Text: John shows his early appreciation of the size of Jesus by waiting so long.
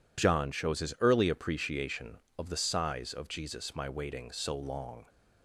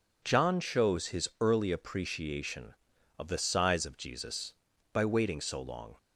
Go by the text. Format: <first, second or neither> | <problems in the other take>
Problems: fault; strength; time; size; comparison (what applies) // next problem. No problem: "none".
second | says "my" for "by"; at 3.7 s